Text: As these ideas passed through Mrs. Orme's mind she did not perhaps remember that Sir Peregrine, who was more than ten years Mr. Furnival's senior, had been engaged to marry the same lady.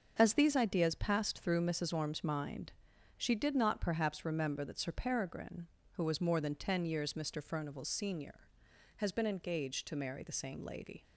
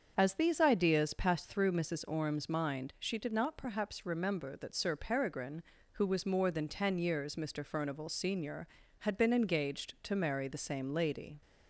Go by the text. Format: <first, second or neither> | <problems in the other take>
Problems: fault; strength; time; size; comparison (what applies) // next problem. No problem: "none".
second | starts louder than the rest; until 1.2 s; 7 dB; also in the second // pauses between "mind" and "she"; noticeable; at 2.7 s; 0.48 s long // says "has" for "had"; at 8.9 s